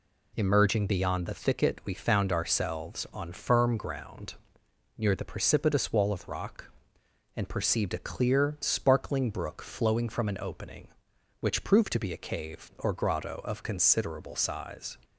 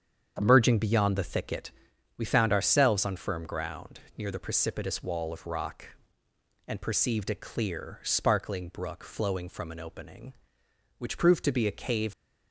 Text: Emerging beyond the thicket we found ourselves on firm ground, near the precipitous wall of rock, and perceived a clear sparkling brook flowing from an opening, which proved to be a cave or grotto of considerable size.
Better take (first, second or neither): first